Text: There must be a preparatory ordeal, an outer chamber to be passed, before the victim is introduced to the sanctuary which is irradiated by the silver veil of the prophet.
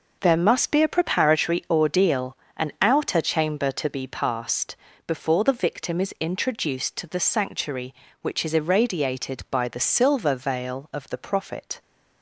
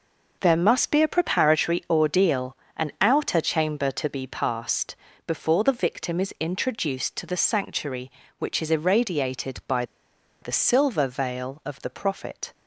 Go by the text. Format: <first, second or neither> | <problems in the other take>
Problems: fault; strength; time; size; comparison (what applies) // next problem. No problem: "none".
first | pauses between "by" and "the"; noticeable; at 9.8 s; 0.57 s long